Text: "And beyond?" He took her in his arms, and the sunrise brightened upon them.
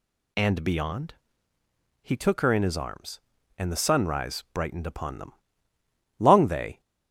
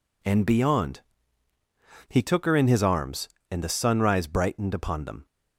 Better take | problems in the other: second | goes on to say "Long they"; noticeable; from 6.1 s on; 0.62 s long

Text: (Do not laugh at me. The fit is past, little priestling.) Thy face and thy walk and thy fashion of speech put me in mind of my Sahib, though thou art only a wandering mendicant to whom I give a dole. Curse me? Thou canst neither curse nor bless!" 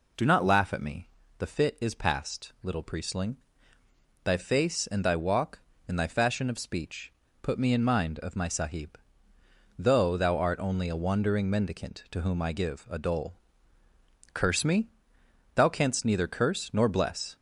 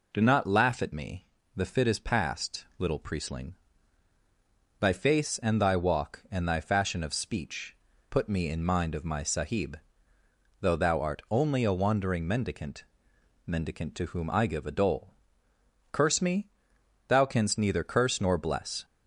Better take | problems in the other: first | pauses between "speech" and "put"; slight; at 7.7 s; 0.36 s long; slight in the first // says "mendicant" twice; at 13.4 s

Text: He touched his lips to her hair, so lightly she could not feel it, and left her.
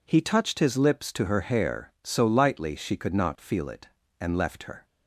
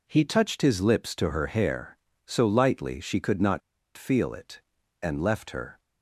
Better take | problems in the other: first | pauses between "not" and "feel"; at 3.6 s; 0.36 s long

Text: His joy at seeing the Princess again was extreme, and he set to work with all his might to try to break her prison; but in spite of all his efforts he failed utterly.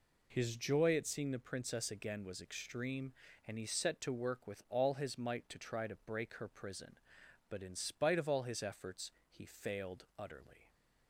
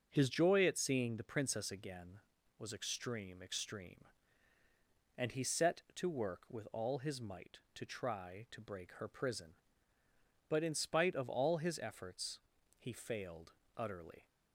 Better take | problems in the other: first | starts louder than the rest; noticeable; until 1.1 s; 6 dB // says "extreme" twice; at 3.4 s // pauses between "efforts" and "he"; at 12.3 s; 0.40 s long; slight in the first // pauses between "failed" and "utterly"; slight; at 13.5 s; 0.26 s long

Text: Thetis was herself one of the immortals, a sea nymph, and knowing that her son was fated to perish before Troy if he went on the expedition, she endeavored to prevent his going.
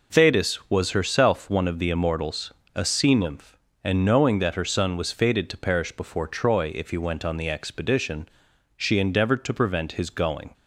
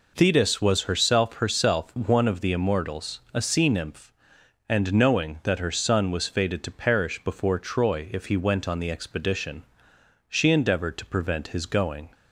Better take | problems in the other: first | says "herself" twice; at 1.3 s

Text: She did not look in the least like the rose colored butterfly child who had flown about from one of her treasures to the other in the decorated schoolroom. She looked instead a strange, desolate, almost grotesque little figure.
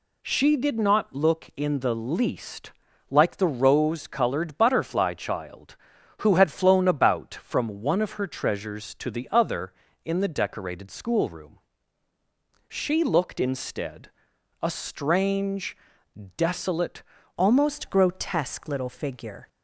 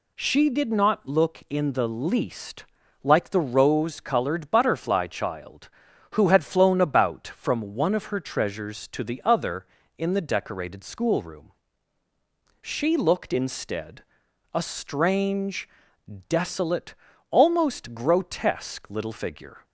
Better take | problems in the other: second | pauses between "least" and "like"; at 2.7 s; 0.38 s long; also in the second // pauses between "instead" and "a"; noticeable; at 14.1 s; 0.50 s long; noticeable in the second // changes voice at "almost"; from 17.3 s on; 2.1 s long

